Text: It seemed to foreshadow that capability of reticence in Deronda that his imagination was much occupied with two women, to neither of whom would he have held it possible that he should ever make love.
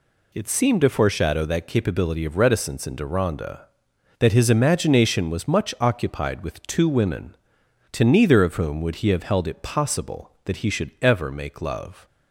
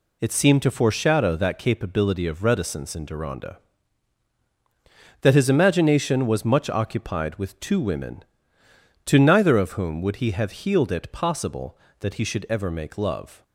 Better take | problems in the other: first | says "healed" for "held"; at 10.5 s

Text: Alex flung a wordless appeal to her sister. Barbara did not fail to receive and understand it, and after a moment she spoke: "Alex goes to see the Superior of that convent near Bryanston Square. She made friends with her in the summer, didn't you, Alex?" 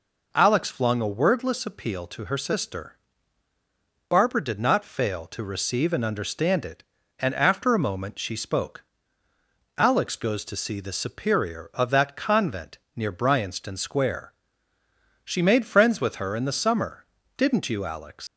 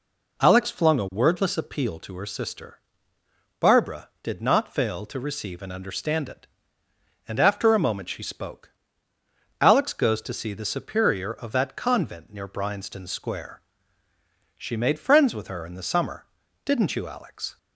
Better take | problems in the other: second | pauses between "convent" and "near"; slight; at 12.7 s; 0.18 s long // leaves "Alex" unfinished; at 18.2 s; 85 ms

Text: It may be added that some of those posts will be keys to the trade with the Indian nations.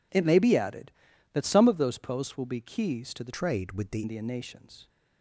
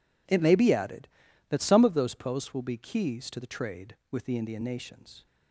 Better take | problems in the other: second | changes voice from "trade" to "the"; from 3.3 to 4.0 s; 0.7 s long

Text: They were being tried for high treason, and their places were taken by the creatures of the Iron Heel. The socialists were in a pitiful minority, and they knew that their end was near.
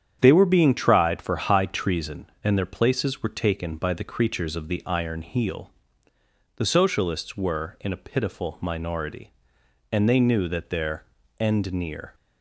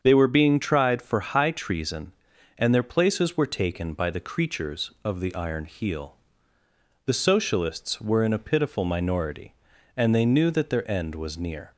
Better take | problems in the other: second | starts louder than the rest; strong; until 1.2 s; 8.5 dB; strong in the second // pauses between "their" and "end"; slight; at 11.0 s; 0.34 s long // skips "was"; at 11.7 s

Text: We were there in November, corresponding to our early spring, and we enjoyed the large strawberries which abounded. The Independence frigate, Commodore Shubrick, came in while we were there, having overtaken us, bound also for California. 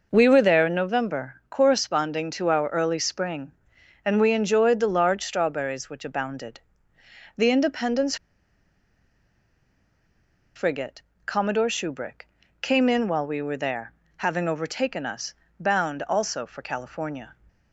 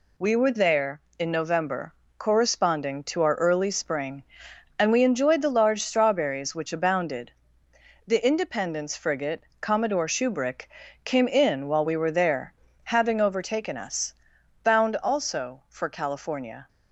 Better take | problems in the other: second | pauses between "Independence" and "frigate"; strong; at 8.1 s; 2.4 s long

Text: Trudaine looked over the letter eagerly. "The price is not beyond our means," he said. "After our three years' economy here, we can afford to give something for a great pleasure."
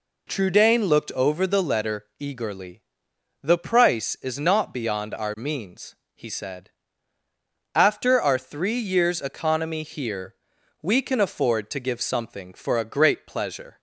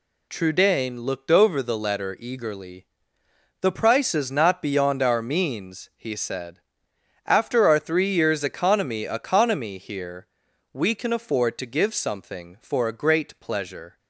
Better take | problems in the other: first | says "economy" twice; at 9.0 s

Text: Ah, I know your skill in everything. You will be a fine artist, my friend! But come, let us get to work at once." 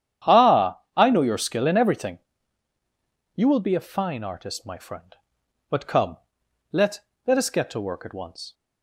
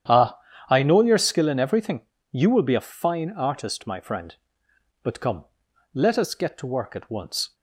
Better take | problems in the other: second | starts louder than the rest; strong; until 1.4 s; 9.5 dB; strong in the second // says "let" twice; at 7.2 s

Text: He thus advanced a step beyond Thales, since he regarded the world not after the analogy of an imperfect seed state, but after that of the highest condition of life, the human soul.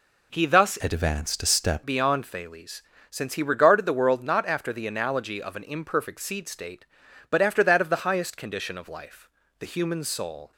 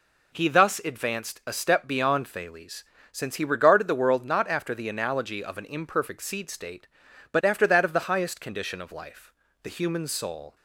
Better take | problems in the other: second | changes voice from "advanced" to "step"; from 0.8 to 1.8 s; 1.0 s long

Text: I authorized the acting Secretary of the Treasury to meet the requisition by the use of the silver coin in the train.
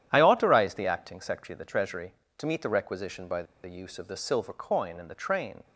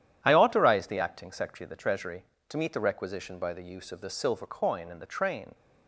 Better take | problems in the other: second | starts louder than the rest; strong; until 1.1 s; 10.5 dB; strong in the second // pauses between "by" and "the"; slight; at 3.4 s; 0.20 s long

